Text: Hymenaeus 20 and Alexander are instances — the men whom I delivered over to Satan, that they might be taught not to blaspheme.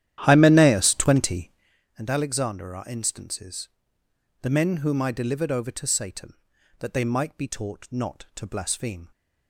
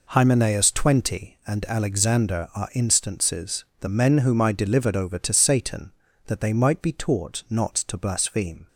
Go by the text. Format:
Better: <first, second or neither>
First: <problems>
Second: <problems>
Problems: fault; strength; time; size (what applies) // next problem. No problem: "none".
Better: second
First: starts louder than the rest; strong; until 1.8 s; 11.5 dB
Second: none